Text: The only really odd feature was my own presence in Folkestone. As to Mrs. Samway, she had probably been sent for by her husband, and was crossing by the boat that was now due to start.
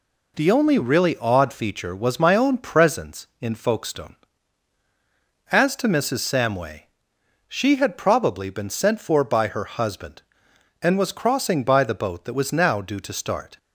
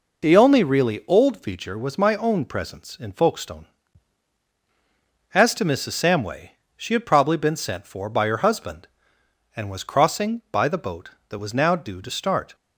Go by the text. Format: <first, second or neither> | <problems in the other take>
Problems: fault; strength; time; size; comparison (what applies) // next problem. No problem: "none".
first | says "old" for "odd"; at 1.0 s